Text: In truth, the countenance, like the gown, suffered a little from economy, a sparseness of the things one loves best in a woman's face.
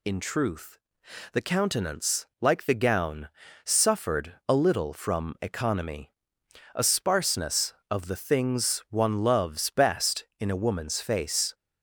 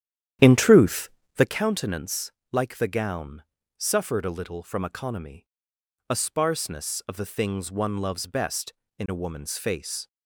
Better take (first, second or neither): first